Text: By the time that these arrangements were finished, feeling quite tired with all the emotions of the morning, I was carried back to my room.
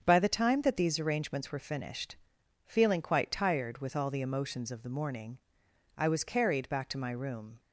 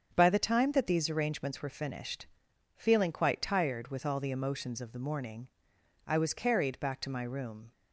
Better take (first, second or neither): neither